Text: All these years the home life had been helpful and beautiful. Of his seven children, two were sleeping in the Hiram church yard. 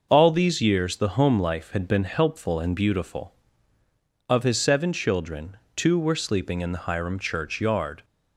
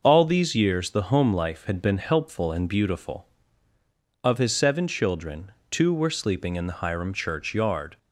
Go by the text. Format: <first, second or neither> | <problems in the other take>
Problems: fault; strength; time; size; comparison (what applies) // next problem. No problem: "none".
neither | none